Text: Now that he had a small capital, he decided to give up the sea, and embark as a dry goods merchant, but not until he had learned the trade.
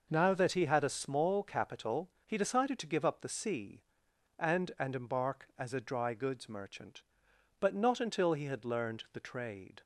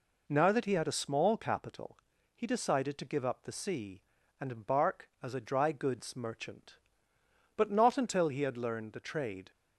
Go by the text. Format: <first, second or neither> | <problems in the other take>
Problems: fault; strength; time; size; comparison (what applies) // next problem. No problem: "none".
second | says "and" twice; at 4.7 s